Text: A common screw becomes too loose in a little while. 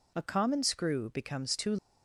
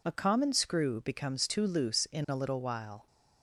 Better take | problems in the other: second | stops before "loose in a little while"; at 1.7 s

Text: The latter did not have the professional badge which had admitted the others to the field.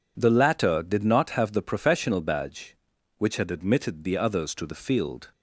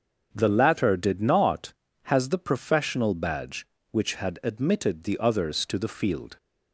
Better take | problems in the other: first | starts louder than the rest; until 1.3 s; 6.5 dB // says "has" for "have"; at 2.0 s

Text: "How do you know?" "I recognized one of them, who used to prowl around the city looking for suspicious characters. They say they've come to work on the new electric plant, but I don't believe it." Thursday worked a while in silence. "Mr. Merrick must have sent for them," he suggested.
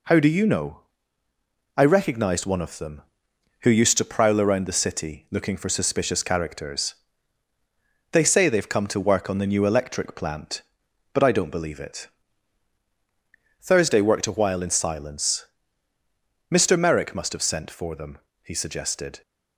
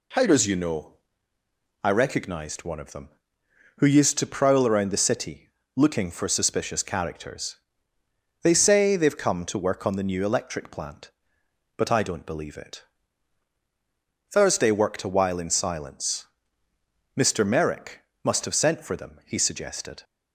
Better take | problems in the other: first | says "does" for "do"; at 0.2 s // pauses between "city" and "looking"; slight; at 5.4 s; 0.26 s long // pauses between "Merrick" and "must"; slight; at 18.0 s; 0.20 s long

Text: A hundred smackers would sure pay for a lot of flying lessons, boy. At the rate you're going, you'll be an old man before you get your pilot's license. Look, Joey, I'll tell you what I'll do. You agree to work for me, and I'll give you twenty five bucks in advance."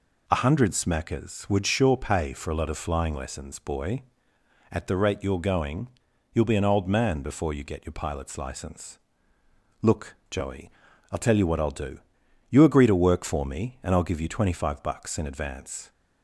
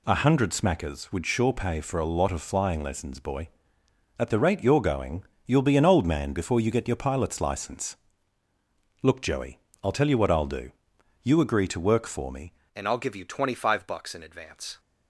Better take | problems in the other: first | changes voice at "and"; from 12.7 s on; 2.0 s long

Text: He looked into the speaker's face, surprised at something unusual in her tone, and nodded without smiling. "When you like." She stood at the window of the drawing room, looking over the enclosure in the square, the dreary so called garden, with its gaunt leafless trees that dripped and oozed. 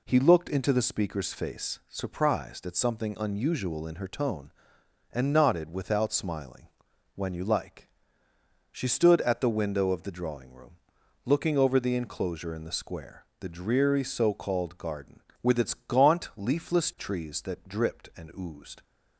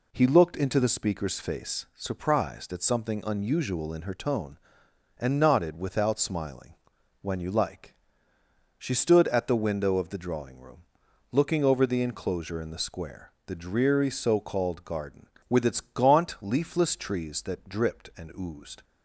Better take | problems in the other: neither | none

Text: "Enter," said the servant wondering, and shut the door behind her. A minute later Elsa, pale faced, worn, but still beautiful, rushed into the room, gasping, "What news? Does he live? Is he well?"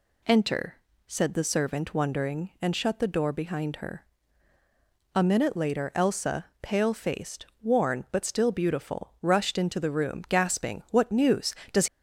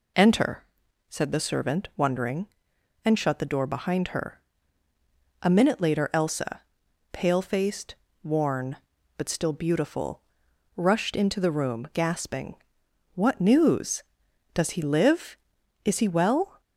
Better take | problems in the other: second | stops before "he live Is he well"; at 11.8 s

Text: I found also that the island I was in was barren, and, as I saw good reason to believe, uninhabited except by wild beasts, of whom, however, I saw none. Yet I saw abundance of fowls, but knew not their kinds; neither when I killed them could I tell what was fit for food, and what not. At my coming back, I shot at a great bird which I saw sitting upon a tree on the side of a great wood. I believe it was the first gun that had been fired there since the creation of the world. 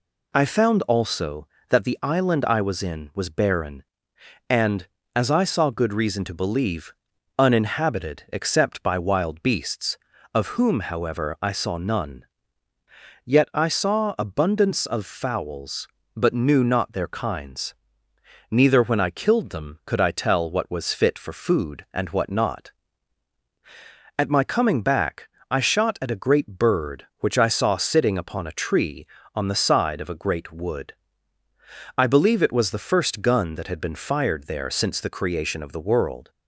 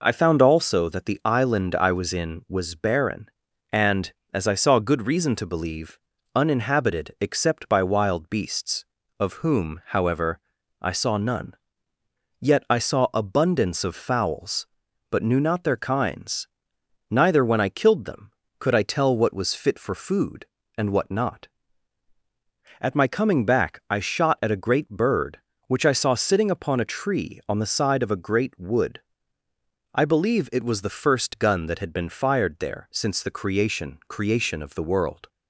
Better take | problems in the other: first | says "creation" twice; at 34.0 s

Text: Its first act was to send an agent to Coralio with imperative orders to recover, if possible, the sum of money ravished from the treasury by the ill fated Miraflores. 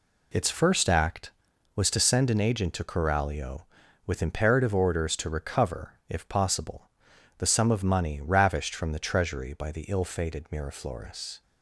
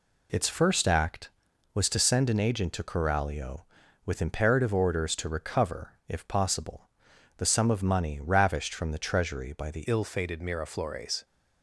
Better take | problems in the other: first | changes voice at "ill"; from 9.8 s on; 1.4 s long

